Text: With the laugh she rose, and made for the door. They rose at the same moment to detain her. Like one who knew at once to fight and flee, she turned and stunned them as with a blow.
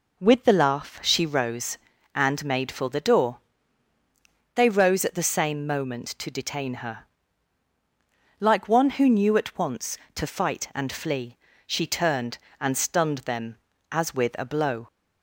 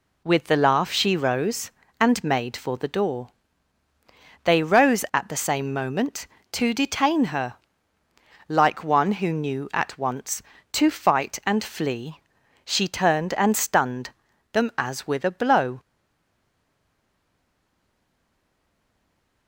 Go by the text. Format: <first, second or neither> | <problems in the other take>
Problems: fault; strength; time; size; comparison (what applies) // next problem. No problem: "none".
first | pauses between "stunned" and "them"; at 14.0 s; 0.42 s long // stays silent after the last word; strong; from 15.7 s on; 3.7 s long